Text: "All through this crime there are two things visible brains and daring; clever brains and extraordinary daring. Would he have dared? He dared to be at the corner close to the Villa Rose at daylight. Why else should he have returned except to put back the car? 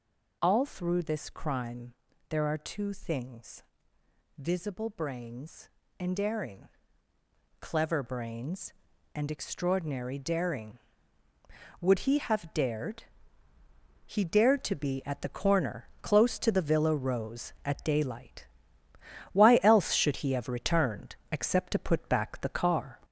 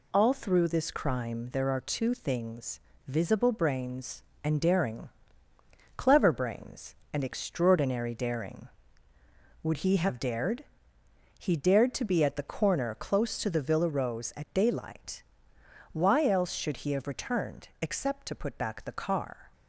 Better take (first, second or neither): second